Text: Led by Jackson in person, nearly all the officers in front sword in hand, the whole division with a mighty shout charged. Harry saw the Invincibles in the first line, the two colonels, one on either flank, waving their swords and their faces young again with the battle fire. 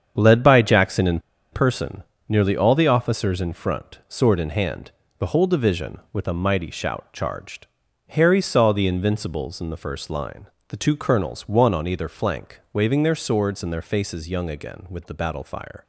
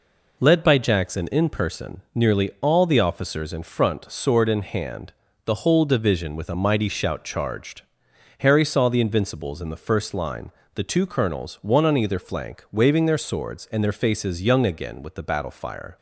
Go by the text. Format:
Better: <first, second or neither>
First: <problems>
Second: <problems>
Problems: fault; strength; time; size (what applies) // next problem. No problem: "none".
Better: second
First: starts louder than the rest; strong; until 1.1 s; 8 dB // pauses between "in" and "person"; slight; at 1.1 s; 0.33 s long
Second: none